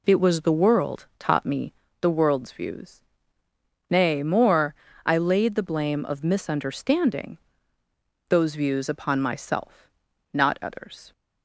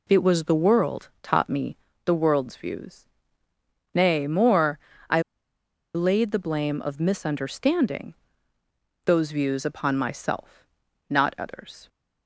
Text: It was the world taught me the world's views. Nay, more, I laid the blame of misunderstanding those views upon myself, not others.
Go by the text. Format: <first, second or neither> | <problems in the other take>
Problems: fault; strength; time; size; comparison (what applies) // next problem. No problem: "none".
first | pauses between "me" and "the"; slight; at 1.7 s; 0.30 s long; slight in the first // pauses between "I" and "laid"; noticeable; at 5.1 s; 0.74 s long // pauses between "misunderstanding" and "those"; noticeable; at 8.1 s; 0.90 s long; noticeable in the first